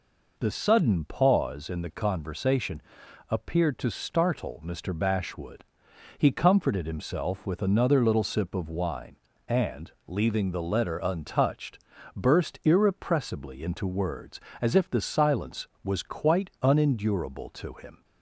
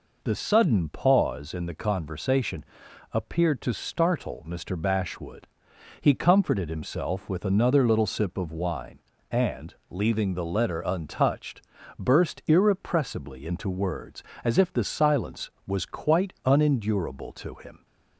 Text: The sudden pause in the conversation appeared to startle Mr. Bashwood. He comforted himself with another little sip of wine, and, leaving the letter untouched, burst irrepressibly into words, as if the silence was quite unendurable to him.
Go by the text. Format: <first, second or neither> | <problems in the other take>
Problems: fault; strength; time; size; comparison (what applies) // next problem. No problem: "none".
neither | pauses between "conversation" and "appeared"; noticeable; the same in both